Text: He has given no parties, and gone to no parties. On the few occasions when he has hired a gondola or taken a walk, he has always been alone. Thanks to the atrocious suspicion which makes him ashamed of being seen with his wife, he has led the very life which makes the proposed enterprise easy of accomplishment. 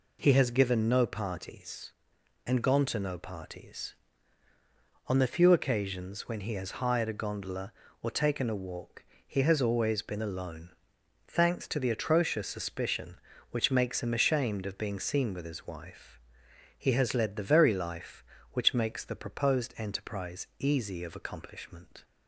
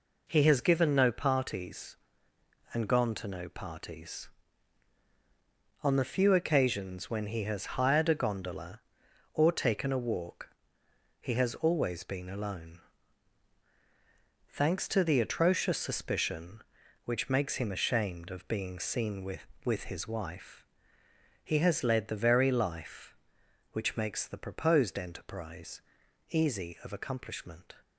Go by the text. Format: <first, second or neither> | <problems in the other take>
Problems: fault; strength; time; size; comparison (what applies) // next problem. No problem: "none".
first | says "with" twice; at 19.6 s // pauses between "enterprise" and "easy"; noticeable; at 25.7 s; 0.48 s long